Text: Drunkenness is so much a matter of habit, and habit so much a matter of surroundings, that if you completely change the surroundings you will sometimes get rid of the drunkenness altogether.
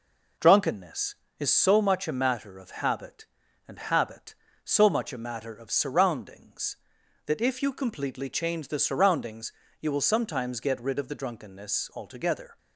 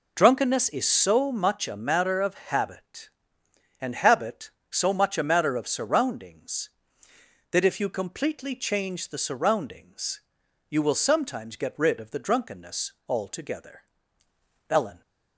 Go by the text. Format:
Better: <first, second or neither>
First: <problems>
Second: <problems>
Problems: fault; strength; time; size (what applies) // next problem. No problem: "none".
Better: first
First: pauses between "surroundings" and "you"; slight; at 9.5 s; 0.30 s long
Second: pauses between "surroundings" and "you"; noticeable; at 10.2 s; 0.48 s long // goes on to say "Ellen"; slight; from 14.6 s on; 0.32 s long